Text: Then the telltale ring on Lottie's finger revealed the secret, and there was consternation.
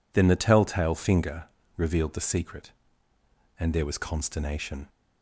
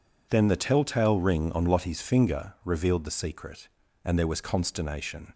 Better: second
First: skips "ring on Lottie's"; at 0.9 s // pauses between "finger" and "revealed"; slight; at 1.4 s; 0.32 s long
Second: none

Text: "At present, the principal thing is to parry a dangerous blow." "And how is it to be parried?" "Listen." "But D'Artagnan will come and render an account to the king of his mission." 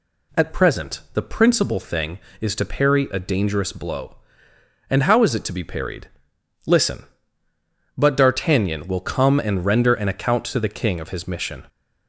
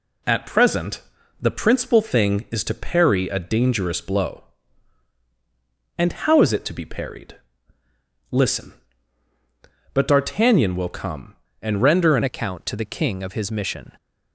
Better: first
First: none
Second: changes voice at "account"; from 12.2 s on; 1.7 s long

